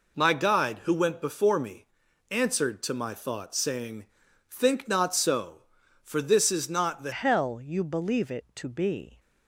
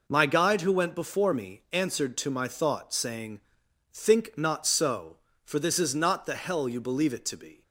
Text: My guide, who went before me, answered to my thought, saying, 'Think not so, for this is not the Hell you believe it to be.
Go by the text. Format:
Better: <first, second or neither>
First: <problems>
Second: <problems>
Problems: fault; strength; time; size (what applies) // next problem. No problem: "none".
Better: second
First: changes voice at "Hell"; from 7.1 s on; 2.0 s long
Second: none